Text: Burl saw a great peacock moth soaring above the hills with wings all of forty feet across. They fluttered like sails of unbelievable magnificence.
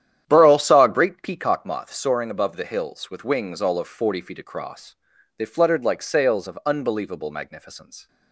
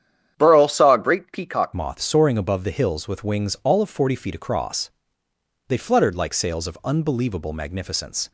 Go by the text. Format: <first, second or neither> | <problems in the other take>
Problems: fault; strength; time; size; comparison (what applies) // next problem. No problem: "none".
first | starts louder than the rest; strong; until 1.3 s; 9.5 dB; strong in the first // changes voice at "moth"; from 1.7 s on; 6.6 s long